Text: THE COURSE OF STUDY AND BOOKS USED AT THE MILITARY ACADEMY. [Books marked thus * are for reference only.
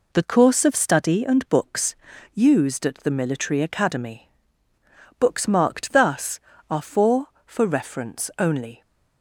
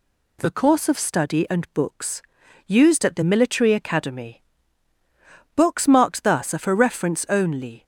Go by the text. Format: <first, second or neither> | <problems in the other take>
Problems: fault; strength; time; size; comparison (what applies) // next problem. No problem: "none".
second | pauses between "BOOKS" and "USED"; at 1.9 s; 0.40 s long; also in the second // says "for" twice; at 7.4 s